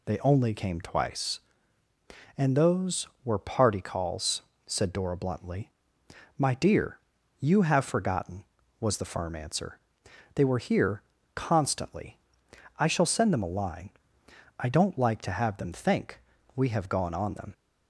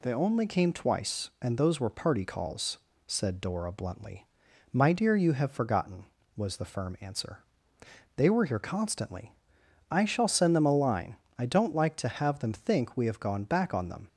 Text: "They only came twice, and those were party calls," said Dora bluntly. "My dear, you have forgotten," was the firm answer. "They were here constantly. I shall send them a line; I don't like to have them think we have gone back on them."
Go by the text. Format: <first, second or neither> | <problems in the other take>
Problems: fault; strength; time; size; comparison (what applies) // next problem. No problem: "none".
second | pauses between "here" and "constantly"; slight; at 11.0 s; 0.32 s long // pauses between "think" and "we"; slight; at 16.1 s; 0.36 s long // skips "back"; at 17.1 s